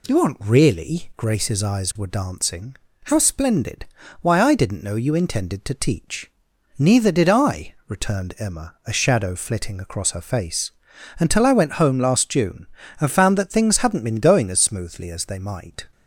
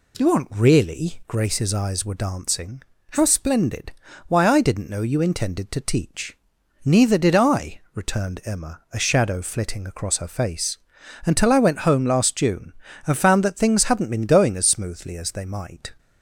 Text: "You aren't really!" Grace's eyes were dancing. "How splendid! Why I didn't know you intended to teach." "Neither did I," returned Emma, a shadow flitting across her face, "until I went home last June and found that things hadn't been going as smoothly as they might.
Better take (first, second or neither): neither